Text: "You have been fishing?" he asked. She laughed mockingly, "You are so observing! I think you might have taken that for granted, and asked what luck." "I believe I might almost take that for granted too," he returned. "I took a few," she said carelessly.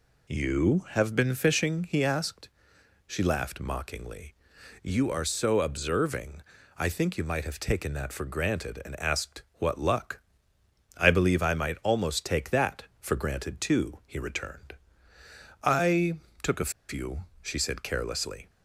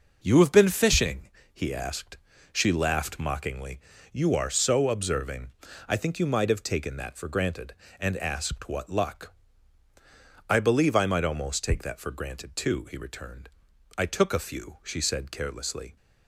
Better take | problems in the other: second | pauses between "I" and "took"; slight; at 16.1 s; 0.24 s long // pauses between "a" and "few"; slight; at 16.7 s; 0.18 s long

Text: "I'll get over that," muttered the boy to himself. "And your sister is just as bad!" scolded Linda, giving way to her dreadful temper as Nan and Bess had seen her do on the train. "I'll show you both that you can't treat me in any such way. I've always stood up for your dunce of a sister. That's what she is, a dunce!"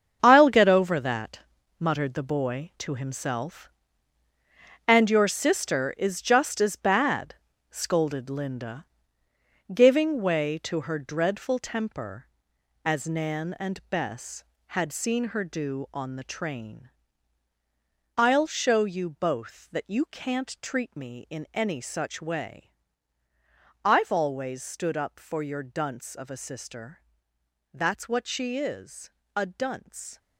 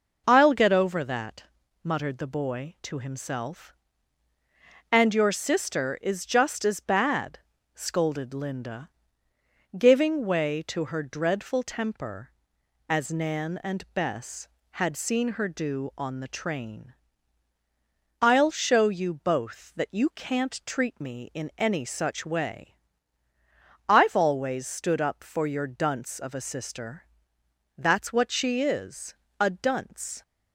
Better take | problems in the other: second | gets quieter; strong; throughout; 11 dB

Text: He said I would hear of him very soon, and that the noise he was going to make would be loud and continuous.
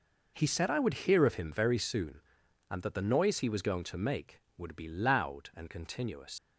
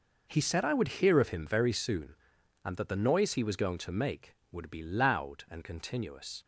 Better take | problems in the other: second | leaves "continuous" unfinished; at 6.3 s; 110 ms

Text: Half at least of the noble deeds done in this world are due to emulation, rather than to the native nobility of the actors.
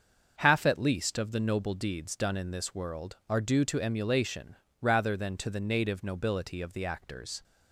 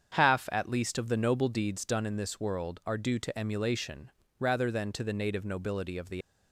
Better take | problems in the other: first | starts louder than the rest; strong; until 1.1 s; 7.5 dB; also in the first // stops before "actors"; at 6.2 s

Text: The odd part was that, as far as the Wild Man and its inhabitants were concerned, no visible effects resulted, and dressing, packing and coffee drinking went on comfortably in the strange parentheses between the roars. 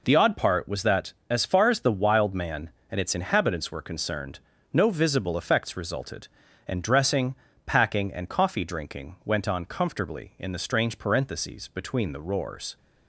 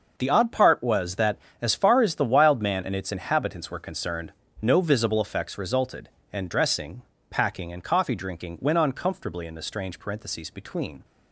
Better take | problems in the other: first | starts louder than the rest; noticeable; until 1.2 s; 6 dB // stops before "the roars"; at 11.0 s

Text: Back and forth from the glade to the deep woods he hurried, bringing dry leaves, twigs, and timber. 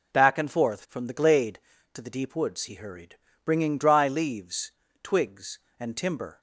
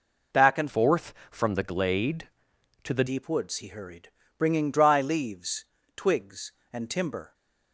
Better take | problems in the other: first | changes voice from "forth" to "the"; from 0.6 to 3.0 s; 2.4 s long

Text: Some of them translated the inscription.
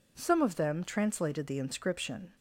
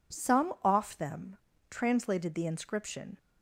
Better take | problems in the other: first | says "off" for "of"; at 0.6 s // pauses between "them" and "translated"; slight; at 1.3 s; 0.32 s long

